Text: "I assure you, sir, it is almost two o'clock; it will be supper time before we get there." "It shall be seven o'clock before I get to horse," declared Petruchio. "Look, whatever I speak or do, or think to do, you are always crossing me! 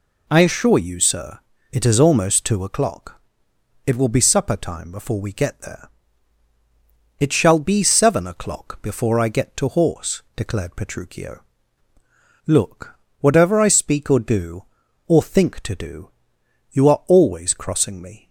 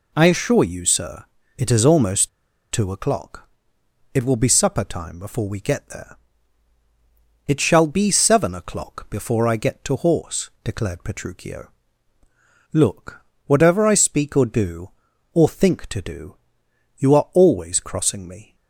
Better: first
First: none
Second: pauses between "almost" and "two"; at 2.2 s; 0.43 s long

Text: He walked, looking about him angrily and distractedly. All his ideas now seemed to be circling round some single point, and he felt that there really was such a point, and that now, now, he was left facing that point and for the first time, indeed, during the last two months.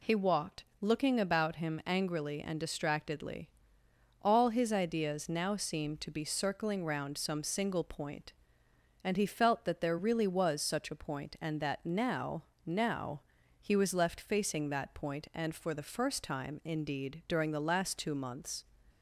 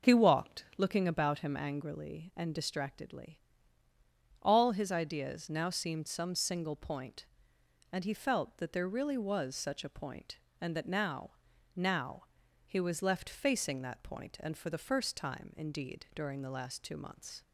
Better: first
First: none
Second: skips "to be circling round"; at 6.0 s

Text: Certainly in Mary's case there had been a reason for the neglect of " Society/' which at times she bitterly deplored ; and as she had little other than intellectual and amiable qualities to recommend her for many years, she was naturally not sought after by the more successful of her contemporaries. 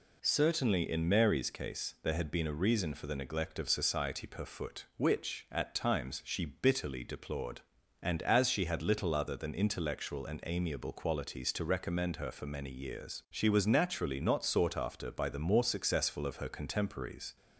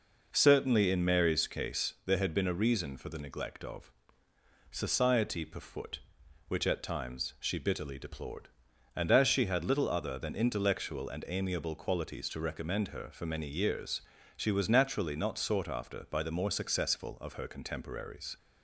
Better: neither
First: none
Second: none

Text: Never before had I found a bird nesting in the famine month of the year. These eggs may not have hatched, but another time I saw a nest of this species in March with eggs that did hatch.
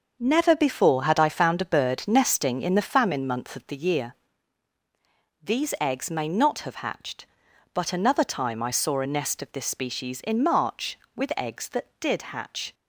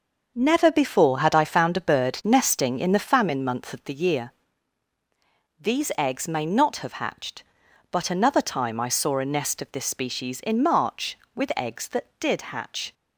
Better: neither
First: starts louder than the rest; noticeable; until 1.2 s; 6 dB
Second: starts louder than the rest; noticeable; until 1.3 s; 6 dB

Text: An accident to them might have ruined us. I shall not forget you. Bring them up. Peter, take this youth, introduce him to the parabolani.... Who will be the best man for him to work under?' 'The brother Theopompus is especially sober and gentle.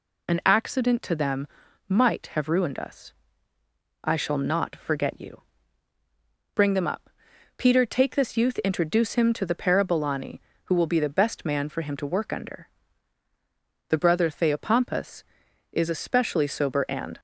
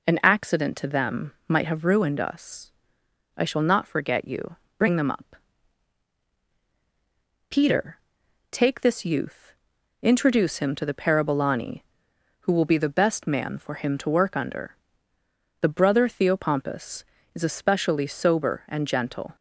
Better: second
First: pauses between "them" and "might"; at 1.4 s; 0.42 s long // stops before "gentle"; at 17.1 s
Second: none

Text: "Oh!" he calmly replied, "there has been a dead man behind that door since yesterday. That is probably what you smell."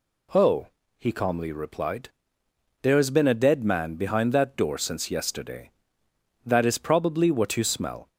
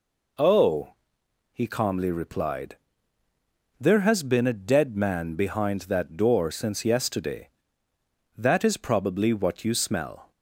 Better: neither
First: none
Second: none

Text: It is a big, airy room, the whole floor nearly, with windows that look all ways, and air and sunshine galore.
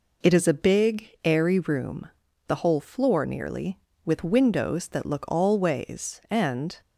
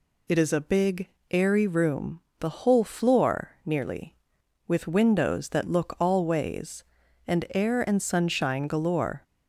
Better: second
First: stops before "air and sunshine galore"; at 6.8 s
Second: none

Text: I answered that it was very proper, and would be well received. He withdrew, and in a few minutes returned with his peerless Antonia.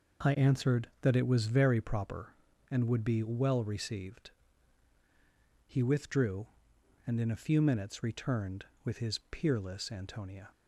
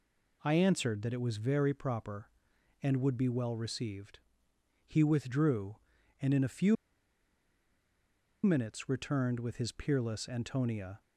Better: first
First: none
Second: pauses between "few" and "minutes"; strong; at 6.7 s; 1.6 s long

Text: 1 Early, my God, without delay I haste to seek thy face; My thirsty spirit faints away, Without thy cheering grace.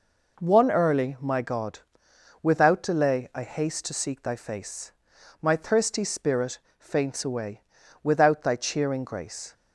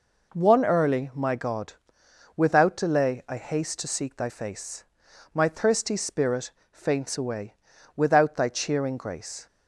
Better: neither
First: pauses between "spirit" and "faints"; slight; at 6.5 s; 0.21 s long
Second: pauses between "spirit" and "faints"; slight; at 6.5 s; 0.22 s long

